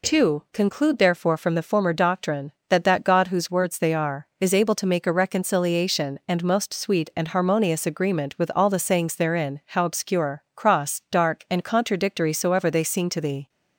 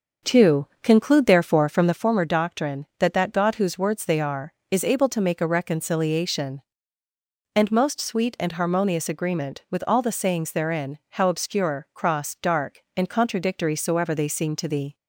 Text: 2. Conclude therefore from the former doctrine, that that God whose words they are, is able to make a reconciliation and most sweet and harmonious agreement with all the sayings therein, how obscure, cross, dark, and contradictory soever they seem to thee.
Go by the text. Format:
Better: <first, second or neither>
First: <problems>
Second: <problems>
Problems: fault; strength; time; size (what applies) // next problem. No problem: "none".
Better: first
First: none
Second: starts louder than the rest; until 2.1 s; 6.5 dB